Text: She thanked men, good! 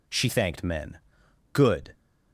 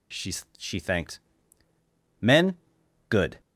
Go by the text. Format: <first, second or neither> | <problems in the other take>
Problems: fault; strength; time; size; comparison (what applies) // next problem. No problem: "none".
first | says "She" twice; at 0.5 s // pauses between "thanked" and "men"; at 1.2 s; 1.0 s long